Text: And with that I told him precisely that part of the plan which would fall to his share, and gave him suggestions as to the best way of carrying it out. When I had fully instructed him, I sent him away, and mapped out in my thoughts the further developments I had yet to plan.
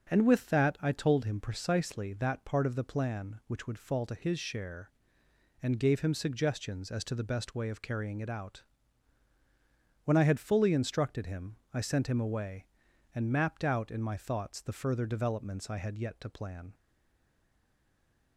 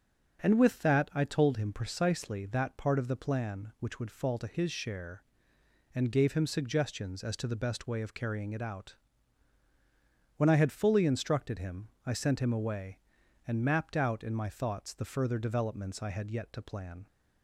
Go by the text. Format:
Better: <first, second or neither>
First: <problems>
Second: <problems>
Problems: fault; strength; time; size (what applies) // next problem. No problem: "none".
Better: second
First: starts louder than the rest; until 1.1 s; 7 dB // stays silent after the last word; noticeable; from 16.7 s on; 1.6 s long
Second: starts louder than the rest; until 1.4 s; 7 dB